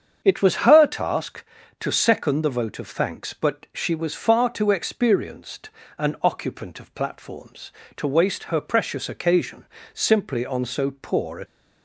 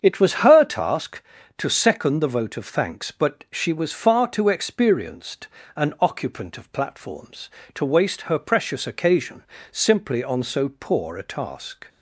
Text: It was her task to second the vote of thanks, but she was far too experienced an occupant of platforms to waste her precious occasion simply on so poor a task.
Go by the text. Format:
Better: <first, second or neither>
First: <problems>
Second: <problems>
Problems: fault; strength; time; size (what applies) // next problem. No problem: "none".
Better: second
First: starts louder than the rest; strong; until 1.2 s; 7.5 dB // pauses between "experienced" and "an"; slight; at 5.7 s; 0.26 s long // pauses between "occasion" and "simply"; slight; at 9.6 s; 0.28 s long // stops before "task"; at 11.4 s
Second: starts louder than the rest; strong; until 1.0 s; 7.5 dB // pauses between "experienced" and "an"; slight; at 5.4 s; 0.26 s long // pauses between "occasion" and "simply"; slight; at 9.4 s; 0.28 s long